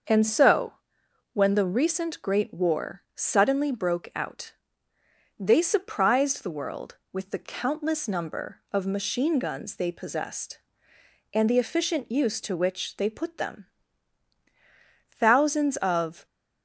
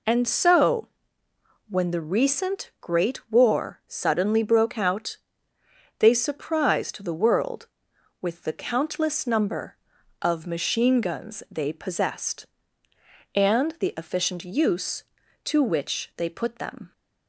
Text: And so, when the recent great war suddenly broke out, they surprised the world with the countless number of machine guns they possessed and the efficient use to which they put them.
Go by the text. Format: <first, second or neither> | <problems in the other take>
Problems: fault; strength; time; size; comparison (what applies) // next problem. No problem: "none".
second | starts louder than the rest; until 1.7 s; 6.5 dB // goes on to say "Thousands of"; noticeable; from 15.1 s on; 1.1 s long